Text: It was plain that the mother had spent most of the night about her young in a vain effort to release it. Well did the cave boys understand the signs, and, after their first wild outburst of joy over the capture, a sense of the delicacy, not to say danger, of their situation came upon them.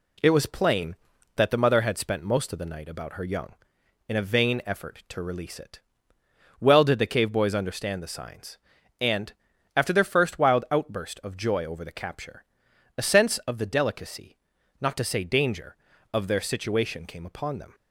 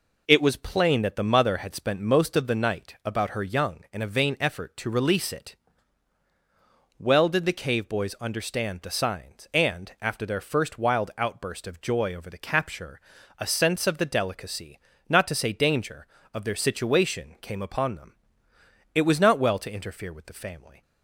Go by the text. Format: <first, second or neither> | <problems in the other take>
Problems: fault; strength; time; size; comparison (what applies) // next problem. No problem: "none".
first | goes on to say "It was not well to interfere with the family"; strong; from 18.9 s on; 1.8 s long